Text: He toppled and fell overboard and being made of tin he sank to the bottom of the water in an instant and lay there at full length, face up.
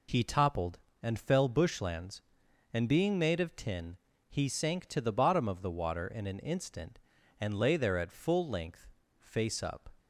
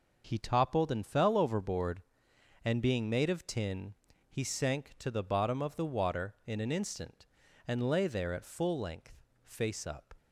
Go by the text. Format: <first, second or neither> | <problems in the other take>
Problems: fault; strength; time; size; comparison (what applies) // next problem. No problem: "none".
second | says "bushlands" for "overboard"; at 1.4 s // pauses between "tin" and "he"; slight; at 3.9 s; 0.32 s long; slight in the second